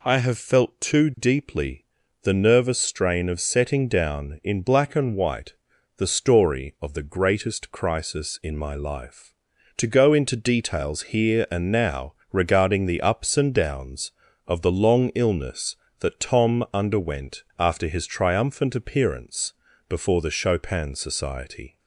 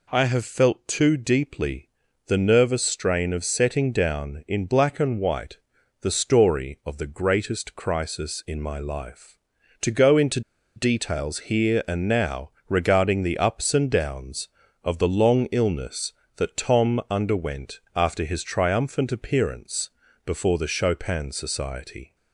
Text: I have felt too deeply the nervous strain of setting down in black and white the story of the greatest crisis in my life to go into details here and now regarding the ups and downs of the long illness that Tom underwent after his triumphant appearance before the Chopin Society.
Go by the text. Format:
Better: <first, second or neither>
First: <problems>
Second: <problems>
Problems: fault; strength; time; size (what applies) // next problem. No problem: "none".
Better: first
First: pauses between "deeply" and "the"; at 1.8 s; 0.38 s long // pauses between "white" and "the"; at 5.5 s; 0.42 s long // pauses between "now" and "regarding"; slight; at 12.1 s; 0.20 s long // pauses between "underwent" and "after"; slight; at 17.4 s; 0.16 s long // pauses between "appearance" and "before"; slight; at 19.5 s; 0.34 s long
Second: pauses between "deeply" and "the"; at 1.9 s; 0.38 s long // pauses between "white" and "the"; at 5.5 s; 0.42 s long // pauses between "into" and "details"; slight; at 10.4 s; 0.35 s long // pauses between "now" and "regarding"; slight; at 12.4 s; 0.20 s long // pauses between "underwent" and "after"; slight; at 17.7 s; 0.16 s long // pauses between "appearance" and "before"; slight; at 19.9 s; 0.34 s long